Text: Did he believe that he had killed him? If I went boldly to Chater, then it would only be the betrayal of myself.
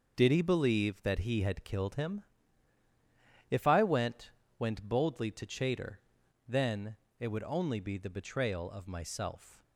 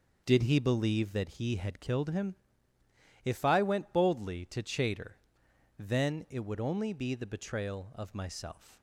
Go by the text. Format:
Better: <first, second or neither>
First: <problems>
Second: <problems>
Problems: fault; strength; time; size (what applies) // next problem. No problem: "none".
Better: second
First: says "went" twice; at 4.5 s // pauses between "then" and "it"; slight; at 6.9 s; 0.22 s long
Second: none